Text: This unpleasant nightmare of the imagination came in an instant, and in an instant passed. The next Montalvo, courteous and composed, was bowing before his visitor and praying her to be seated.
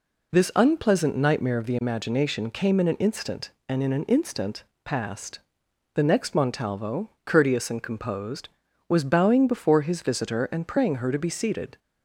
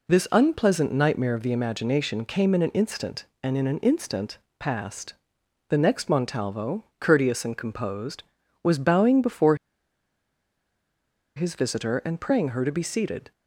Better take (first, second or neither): first